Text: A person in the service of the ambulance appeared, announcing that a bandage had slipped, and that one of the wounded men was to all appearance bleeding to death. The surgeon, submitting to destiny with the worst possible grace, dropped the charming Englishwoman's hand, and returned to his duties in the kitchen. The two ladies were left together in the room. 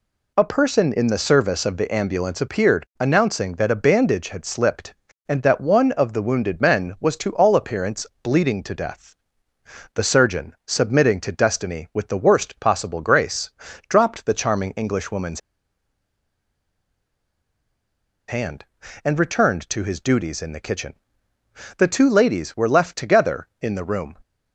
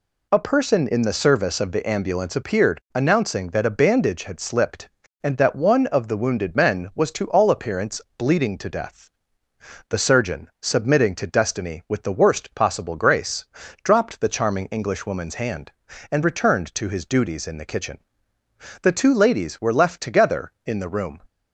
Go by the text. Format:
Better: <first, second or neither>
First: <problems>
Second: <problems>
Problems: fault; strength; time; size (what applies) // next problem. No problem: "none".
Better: second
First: pauses between "appearance" and "bleeding"; slight; at 8.0 s; 0.16 s long // pauses between "Englishwoman's" and "hand"; strong; at 15.4 s; 2.8 s long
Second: pauses between "appearance" and "bleeding"; slight; at 8.0 s; 0.16 s long